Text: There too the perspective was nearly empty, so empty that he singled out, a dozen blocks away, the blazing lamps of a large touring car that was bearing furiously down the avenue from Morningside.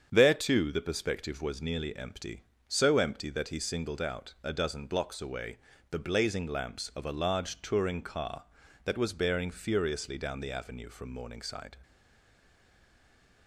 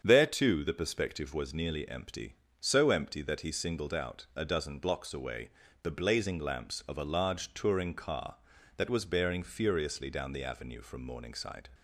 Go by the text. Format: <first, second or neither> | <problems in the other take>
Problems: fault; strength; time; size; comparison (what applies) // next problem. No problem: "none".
second | starts louder than the rest; strong; until 1.1 s; 7.5 dB; strong in the second // stays silent after the last word; noticeable; from 11.8 s on; 1.6 s long